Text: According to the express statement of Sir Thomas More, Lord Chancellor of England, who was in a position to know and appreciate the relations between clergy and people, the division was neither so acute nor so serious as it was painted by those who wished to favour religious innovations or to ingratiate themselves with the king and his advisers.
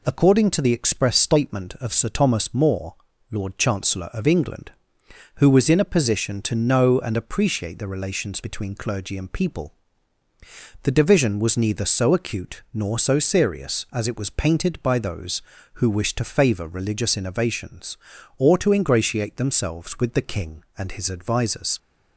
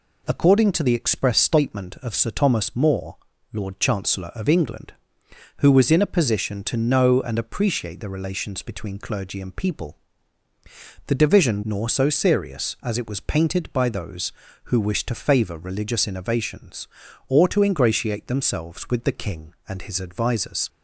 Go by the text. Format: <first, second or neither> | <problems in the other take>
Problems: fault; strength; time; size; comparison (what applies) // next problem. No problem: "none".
first | skips "was neither so acute"; at 11.6 s